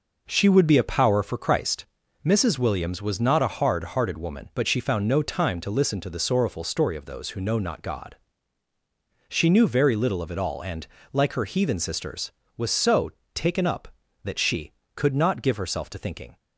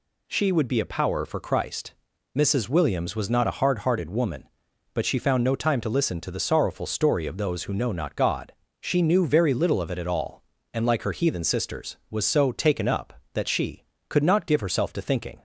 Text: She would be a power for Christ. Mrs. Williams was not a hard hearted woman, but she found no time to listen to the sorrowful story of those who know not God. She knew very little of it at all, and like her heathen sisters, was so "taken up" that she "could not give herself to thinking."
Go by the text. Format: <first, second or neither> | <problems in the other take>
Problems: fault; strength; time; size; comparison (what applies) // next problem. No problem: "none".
second | skips "at"; at 10.3 s // pauses between "and" and "like"; slight; at 10.8 s; 0.26 s long // pauses between "so" and "taken"; slight; at 13.0 s; 0.24 s long